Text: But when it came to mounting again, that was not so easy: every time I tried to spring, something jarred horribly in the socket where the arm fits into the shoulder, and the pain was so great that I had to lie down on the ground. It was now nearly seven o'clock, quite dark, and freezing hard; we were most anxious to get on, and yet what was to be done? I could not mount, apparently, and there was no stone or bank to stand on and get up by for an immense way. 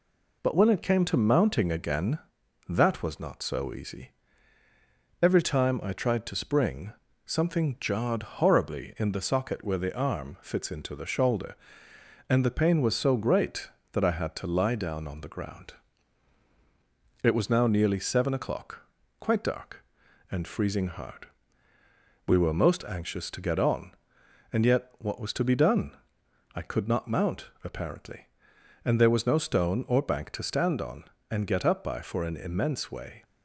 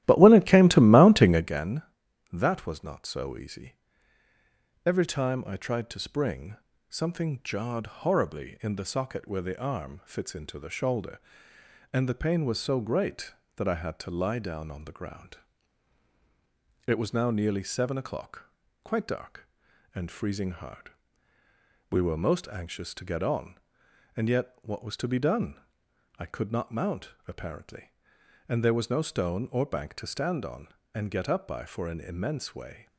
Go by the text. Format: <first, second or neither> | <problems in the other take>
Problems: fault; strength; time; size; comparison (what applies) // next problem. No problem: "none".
first | starts louder than the rest; strong; until 1.6 s; 14 dB // pauses between "jarred" and "horribly"; slight; at 7.8 s; 0.16 s long; slight in the first